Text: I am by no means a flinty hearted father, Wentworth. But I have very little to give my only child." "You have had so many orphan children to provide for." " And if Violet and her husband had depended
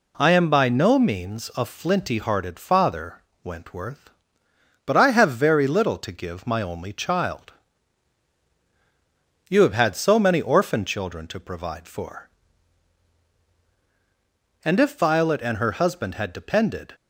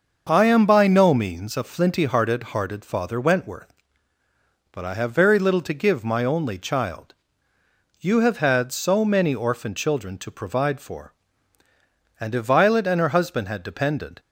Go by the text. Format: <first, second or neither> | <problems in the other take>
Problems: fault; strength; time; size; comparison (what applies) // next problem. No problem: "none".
first | starts louder than the rest; noticeable; until 1.2 s; 6 dB // says "hearted" twice; at 2.5 s